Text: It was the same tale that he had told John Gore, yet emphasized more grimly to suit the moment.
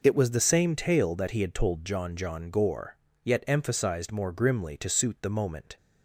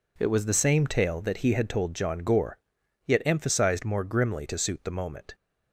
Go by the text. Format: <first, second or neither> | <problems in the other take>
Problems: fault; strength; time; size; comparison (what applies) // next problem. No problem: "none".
second | says "John" twice; at 2.1 s